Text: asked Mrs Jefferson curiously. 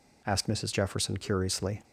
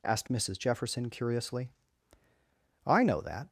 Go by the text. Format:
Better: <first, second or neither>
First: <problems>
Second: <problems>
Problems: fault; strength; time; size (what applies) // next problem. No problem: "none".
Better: first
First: none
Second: goes on to say "I know that"; noticeable; from 2.8 s on; 0.62 s long